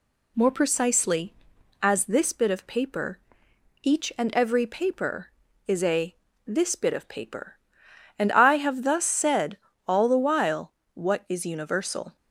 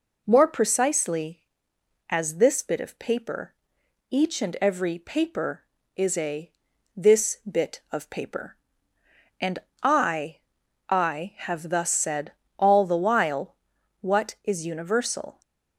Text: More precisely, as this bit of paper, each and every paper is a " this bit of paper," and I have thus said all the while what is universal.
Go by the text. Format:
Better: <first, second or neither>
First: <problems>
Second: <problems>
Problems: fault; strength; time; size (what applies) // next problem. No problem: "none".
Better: first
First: pauses between "said" and "all"; slight; at 9.5 s; 0.28 s long // pauses between "while" and "what"; slight; at 10.7 s; 0.22 s long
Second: pauses between "and" and "I"; slight; at 9.5 s; 0.22 s long // says "I" twice; at 10.8 s // pauses between "said" and "all"; slight; at 12.3 s; 0.26 s long // pauses between "while" and "what"; at 13.5 s; 0.42 s long